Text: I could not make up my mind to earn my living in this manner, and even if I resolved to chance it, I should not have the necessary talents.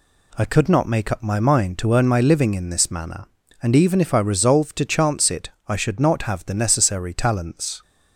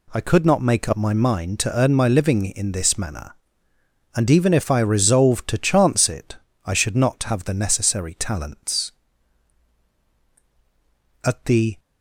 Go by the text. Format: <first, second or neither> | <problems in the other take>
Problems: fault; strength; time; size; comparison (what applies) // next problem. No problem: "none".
first | goes on to say "At the"; from 11.2 s on; 0.54 s long